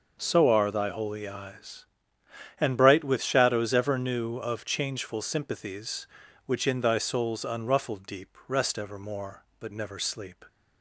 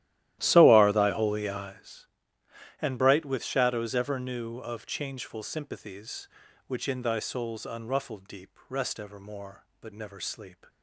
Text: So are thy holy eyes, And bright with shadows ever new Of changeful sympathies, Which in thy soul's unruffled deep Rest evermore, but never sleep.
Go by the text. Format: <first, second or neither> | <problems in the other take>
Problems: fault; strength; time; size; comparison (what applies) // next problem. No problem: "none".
first | starts louder than the rest; strong; until 1.7 s; 14 dB